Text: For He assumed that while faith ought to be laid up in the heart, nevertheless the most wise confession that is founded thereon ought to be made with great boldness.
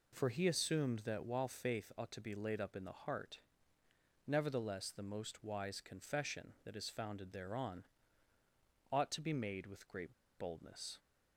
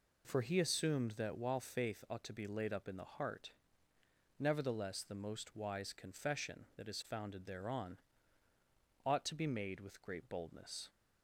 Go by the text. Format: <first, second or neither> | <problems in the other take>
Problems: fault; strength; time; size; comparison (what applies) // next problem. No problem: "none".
second | pauses between "thereon" and "ought"; at 7.8 s; 1.0 s long; also in the second // pauses between "great" and "boldness"; slight; at 10.1 s; 0.23 s long